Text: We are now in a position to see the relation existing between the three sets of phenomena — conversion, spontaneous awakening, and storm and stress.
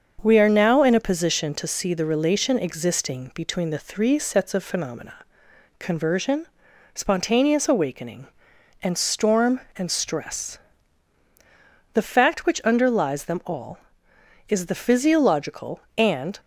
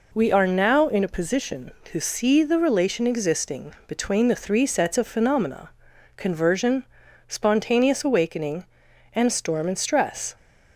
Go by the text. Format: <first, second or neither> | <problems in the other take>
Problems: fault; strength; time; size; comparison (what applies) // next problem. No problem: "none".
second | starts louder than the rest; until 1.2 s; 6.5 dB // goes on to say "The fact which underlies them all is the physiological and"; strong; from 11.9 s on; 4.4 s long